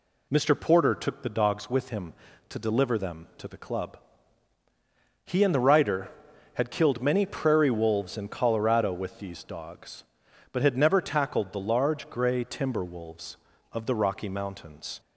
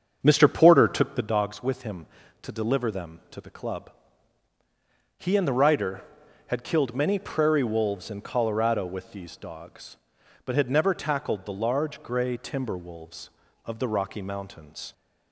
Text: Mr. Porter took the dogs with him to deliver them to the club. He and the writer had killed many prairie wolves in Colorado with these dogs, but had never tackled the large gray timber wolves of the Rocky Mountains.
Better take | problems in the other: first | starts louder than the rest; strong; until 1.3 s; 7 dB

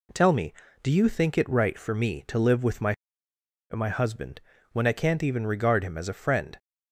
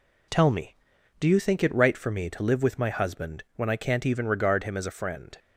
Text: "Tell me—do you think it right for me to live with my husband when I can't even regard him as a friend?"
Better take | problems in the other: second | says "my" twice; at 3.7 s // pauses between "husband" and "when"; slight; at 4.3 s; 0.32 s long

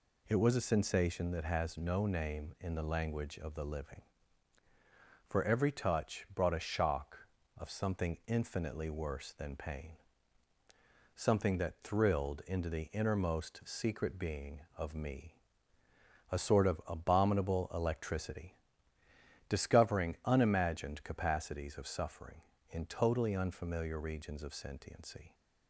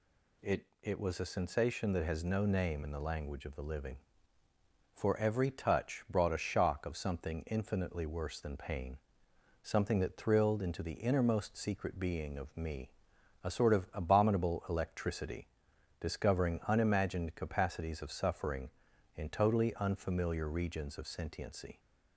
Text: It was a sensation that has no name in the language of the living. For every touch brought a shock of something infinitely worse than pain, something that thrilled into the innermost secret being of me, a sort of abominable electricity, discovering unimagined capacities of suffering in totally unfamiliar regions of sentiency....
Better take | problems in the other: first | says "It" twice; at 0.8 s

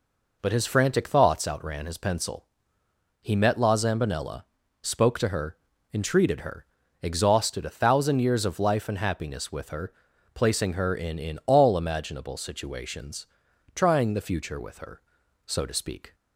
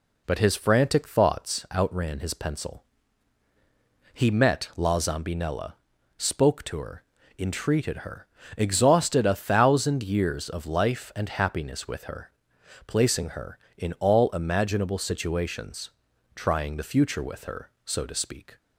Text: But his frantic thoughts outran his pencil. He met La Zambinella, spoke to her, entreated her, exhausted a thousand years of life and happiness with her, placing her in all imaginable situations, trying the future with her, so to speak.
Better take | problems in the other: second | says "in" twice; at 11.1 s

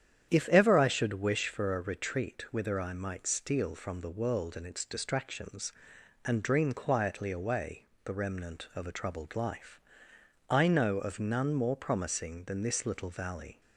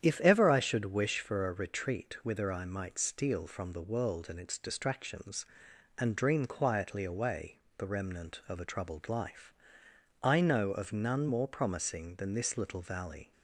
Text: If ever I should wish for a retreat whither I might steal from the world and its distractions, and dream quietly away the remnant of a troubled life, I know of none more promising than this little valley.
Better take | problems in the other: neither | starts louder than the rest; strong; the same in both // pauses between "away" and "the"; slight; the same in both

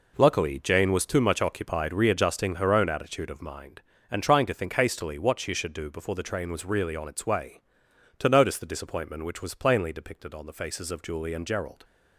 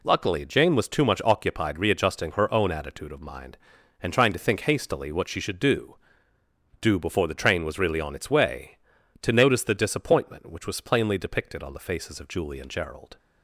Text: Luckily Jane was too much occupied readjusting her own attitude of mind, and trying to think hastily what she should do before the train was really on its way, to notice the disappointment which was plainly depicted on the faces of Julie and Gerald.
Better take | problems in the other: first | says "do" twice; at 6.8 s

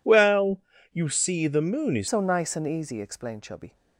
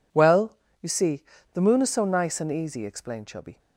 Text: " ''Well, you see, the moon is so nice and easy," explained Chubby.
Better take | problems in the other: second | changes voice from "Well" to "is"; from 0.0 to 2.0 s; 2.0 s long

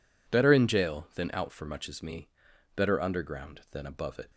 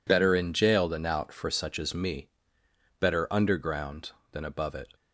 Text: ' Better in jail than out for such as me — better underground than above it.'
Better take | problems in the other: second | says "much" for "such"; at 1.6 s

